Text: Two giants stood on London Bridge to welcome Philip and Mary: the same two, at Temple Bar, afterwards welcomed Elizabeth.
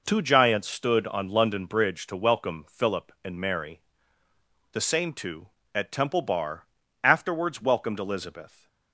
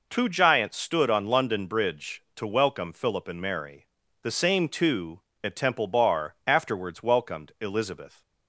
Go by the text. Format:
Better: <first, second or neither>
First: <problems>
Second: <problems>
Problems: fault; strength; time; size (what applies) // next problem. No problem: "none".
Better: neither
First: none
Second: none